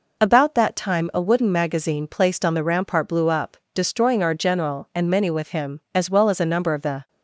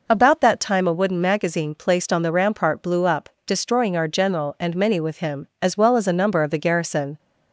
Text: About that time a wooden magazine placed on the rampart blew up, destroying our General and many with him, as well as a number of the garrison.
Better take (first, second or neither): second